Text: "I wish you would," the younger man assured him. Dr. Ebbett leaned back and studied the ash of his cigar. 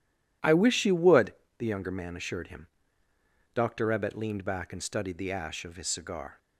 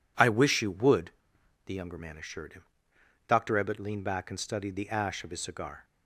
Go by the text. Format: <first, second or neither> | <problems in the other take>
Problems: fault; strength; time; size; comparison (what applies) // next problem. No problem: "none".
neither | none